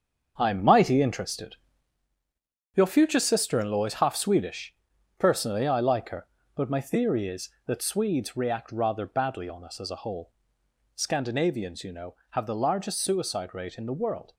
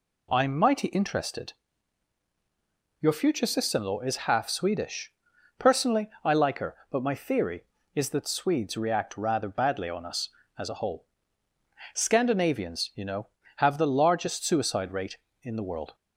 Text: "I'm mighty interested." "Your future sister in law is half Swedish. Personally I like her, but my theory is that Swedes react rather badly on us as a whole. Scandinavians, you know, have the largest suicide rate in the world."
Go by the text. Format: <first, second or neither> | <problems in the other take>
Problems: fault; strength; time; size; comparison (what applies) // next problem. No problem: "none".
second | gets quieter; strong; throughout; 9 dB